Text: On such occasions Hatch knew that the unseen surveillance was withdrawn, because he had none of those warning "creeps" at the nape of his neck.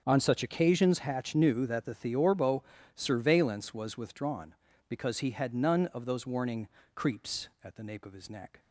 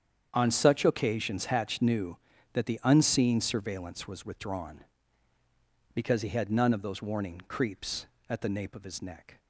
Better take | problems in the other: second | starts louder than the rest; until 1.0 s; 7 dB; strong in the second // says "theorbo" for "unseen"; at 1.9 s // pauses between "warning" and "creeps"; slight; at 6.6 s; 0.26 s long

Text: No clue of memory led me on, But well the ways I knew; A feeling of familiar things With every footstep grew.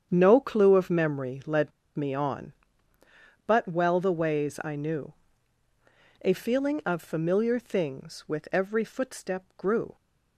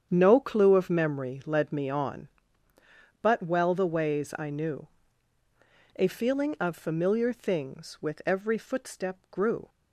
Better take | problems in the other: second | starts louder than the rest; strong; until 1.1 s; 8 dB; strong in the second // pauses between "led" and "me"; slight; at 1.7 s; 0.24 s long

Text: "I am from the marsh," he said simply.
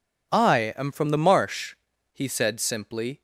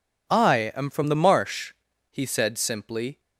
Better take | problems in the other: neither | none

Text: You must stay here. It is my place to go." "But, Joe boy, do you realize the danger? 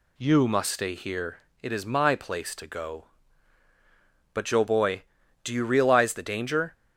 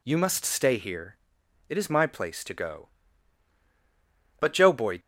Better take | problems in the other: first | stops before "do you realize the danger"; at 4.9 s

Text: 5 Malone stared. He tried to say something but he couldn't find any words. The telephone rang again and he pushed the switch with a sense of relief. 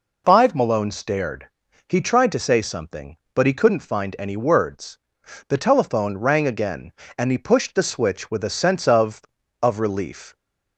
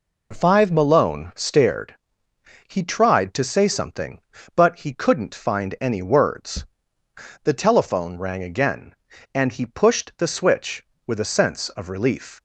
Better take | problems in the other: second | says "of" twice; at 9.6 s

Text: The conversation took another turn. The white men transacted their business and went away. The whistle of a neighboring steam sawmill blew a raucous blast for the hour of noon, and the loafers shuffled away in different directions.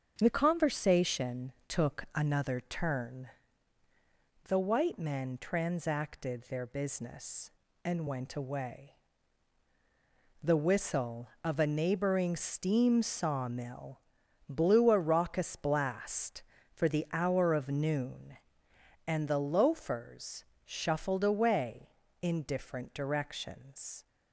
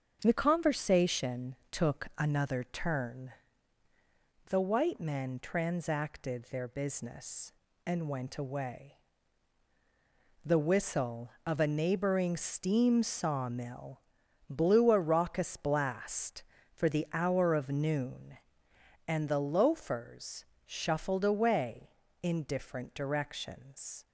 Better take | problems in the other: neither | starts louder than the rest; the same in both // pauses between "conversation" and "took"; slight; the same in both // pauses between "sawmill" and "blew"; noticeable; the same in both // pauses between "loafers" and "shuffled"; slight; the same in both

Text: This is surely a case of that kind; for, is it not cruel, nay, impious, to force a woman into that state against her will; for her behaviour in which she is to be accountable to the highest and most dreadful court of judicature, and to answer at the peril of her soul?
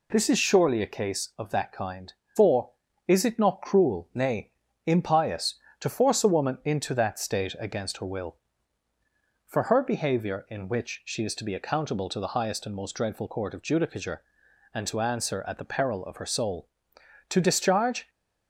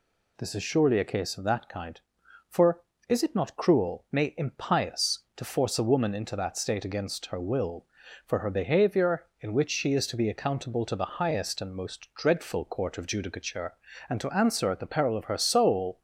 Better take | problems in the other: second | goes on to say "To discharge"; noticeable; from 17.2 s on; 0.80 s long

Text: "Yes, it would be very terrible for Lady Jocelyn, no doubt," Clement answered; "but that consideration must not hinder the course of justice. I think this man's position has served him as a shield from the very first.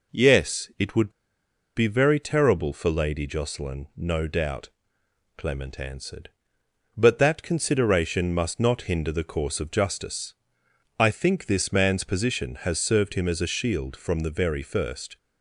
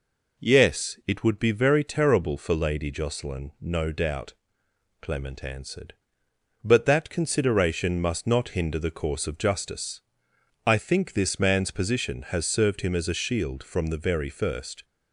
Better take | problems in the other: second | pauses between "would" and "be"; noticeable; at 1.1 s; 0.64 s long

